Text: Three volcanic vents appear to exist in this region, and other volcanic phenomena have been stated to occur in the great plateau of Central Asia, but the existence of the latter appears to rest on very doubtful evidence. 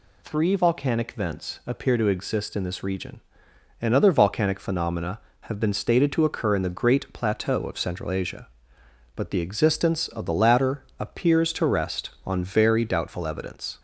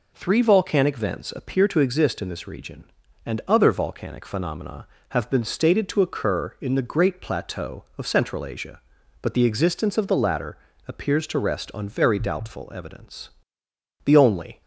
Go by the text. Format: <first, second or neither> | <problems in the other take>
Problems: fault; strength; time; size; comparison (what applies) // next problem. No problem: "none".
first | pauses between "latter" and "appears"; slight; at 10.5 s; 0.30 s long // goes on to say "The only"; from 14.0 s on; 0.56 s long